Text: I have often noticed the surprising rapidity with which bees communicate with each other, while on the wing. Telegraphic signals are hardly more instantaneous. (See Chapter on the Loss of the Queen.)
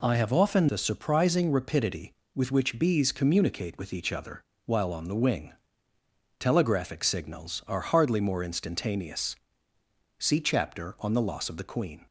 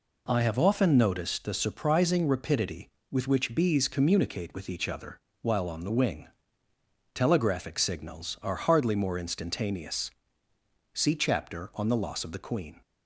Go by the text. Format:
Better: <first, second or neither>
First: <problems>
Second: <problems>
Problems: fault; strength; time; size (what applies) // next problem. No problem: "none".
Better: second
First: skips "noticed"; at 0.6 s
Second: none